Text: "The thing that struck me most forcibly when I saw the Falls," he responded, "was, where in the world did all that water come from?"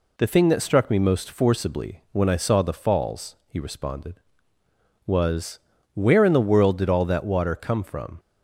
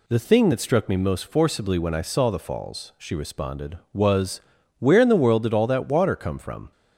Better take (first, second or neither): first